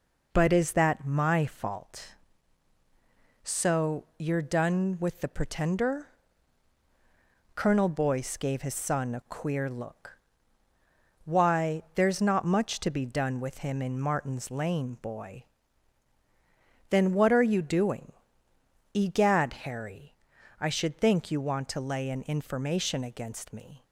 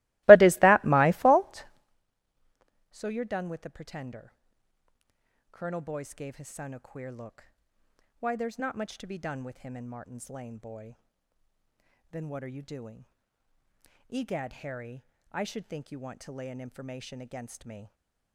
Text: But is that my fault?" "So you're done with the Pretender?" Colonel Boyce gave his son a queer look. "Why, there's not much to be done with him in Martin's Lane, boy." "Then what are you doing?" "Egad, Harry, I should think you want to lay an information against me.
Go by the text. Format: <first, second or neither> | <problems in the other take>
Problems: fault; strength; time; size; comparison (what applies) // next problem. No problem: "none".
first | starts louder than the rest; strong; until 2.0 s; 21 dB